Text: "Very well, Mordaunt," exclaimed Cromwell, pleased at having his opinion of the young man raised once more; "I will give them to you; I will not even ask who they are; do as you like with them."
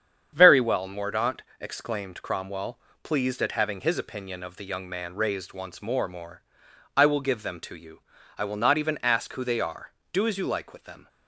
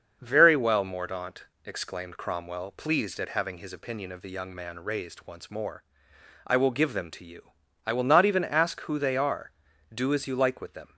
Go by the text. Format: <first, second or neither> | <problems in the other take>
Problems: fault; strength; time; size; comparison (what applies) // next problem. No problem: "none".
second | starts louder than the rest; strong; until 1.3 s; 8 dB; also in the second // says "more" twice; at 6.0 s